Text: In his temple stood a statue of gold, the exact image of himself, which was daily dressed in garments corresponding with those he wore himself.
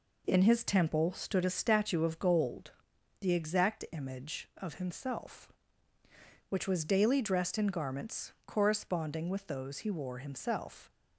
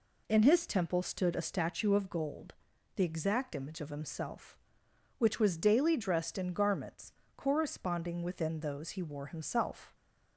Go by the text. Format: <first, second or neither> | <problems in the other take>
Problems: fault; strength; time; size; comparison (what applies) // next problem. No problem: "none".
first | pauses between "garments" and "corresponding"; slight; at 7.1 s; 0.24 s long; slight in the first // says "within" for "with"; at 8.2 s